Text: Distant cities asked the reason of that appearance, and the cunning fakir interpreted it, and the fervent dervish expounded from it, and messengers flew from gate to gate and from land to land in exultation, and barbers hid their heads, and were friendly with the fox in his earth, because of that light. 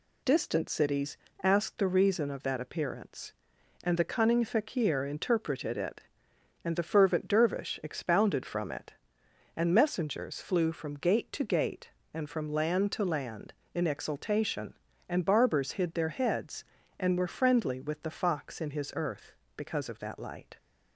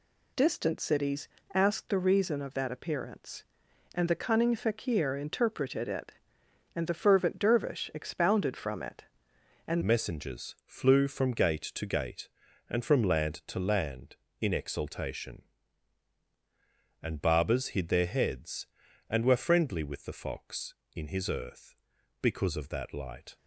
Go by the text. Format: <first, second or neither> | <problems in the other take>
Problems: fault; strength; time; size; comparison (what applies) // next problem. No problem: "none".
first | pauses between "cities" and "asked"; slight; at 1.2 s; 0.26 s long; slight in the first // changes voice at "messengers"; from 9.8 s on; 13.5 s long